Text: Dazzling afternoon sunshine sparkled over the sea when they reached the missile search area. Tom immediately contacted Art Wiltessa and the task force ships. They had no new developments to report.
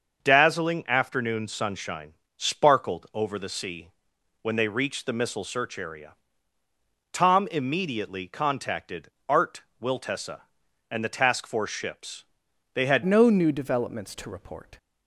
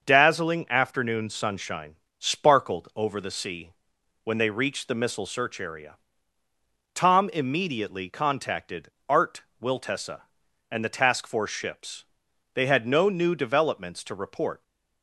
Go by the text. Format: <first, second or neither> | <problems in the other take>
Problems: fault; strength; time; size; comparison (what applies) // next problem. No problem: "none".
second | starts louder than the rest; until 1.2 s; 6.5 dB; also in the second // pauses between "sunshine" and "sparkled"; slight; at 2.1 s; 0.24 s long; slight in the second // pauses between "sea" and "when"; noticeable; at 3.8 s; 0.54 s long; noticeable in the second // pauses between "contacted" and "Art"; slight; at 9.0 s; 0.22 s long; slight in the second // pauses between "Art" and "Wiltessa"; slight; at 9.6 s; 0.20 s long; slight in the second // changes voice at "no"; from 13.0 s on; 1.7 s long